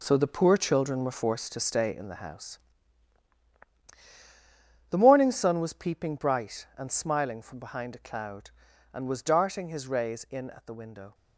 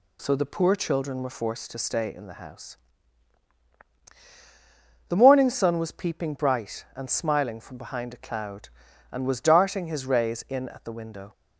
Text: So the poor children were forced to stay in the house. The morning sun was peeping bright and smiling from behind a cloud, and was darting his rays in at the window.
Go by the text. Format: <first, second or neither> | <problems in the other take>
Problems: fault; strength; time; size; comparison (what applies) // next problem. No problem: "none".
second | gets quieter; strong; throughout; 10 dB